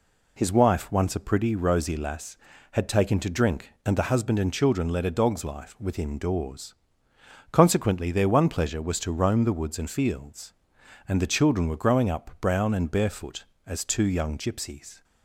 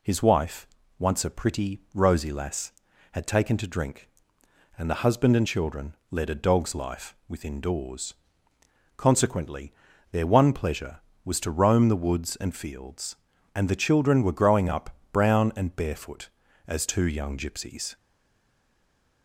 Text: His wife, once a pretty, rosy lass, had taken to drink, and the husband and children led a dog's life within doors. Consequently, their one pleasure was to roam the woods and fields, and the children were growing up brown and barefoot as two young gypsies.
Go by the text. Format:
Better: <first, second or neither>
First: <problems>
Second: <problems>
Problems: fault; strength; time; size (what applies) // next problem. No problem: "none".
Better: first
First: none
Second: pauses between "children" and "led"; slight; at 5.9 s; 0.16 s long // pauses between "up" and "brown"; slight; at 14.8 s; 0.22 s long // stays silent after the last word; noticeable; from 17.9 s on; 1.3 s long